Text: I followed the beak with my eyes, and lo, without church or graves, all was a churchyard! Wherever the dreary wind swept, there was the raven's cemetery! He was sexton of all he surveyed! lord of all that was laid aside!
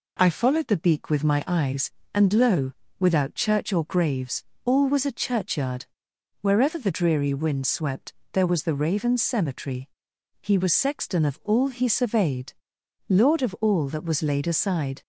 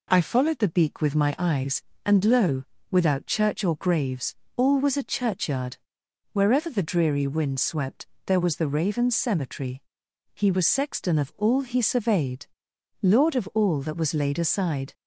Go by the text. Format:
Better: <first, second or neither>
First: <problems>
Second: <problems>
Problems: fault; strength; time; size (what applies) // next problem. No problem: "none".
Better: neither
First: none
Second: none